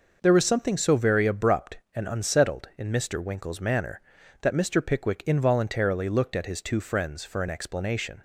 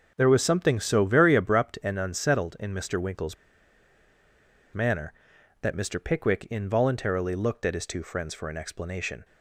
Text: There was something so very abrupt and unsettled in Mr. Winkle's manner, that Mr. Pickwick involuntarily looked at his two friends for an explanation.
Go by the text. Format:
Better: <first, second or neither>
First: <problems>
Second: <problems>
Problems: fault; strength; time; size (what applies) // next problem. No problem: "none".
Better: first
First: none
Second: pauses between "Winkle's" and "manner"; strong; at 3.3 s; 1.3 s long